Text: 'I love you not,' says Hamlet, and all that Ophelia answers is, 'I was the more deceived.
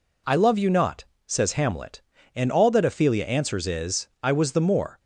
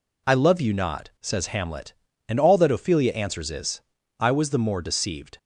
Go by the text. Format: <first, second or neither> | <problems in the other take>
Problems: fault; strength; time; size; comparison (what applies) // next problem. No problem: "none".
second | stops before "deceived"; at 4.9 s